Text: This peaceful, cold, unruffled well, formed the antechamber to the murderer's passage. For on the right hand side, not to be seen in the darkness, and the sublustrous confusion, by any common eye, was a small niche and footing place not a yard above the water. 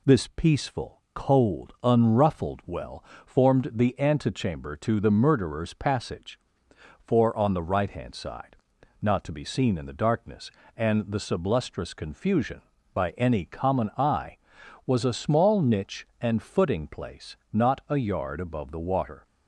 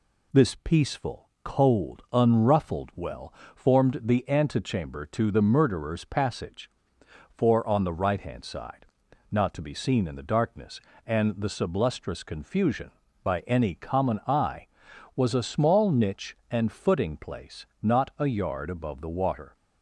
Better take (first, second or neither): neither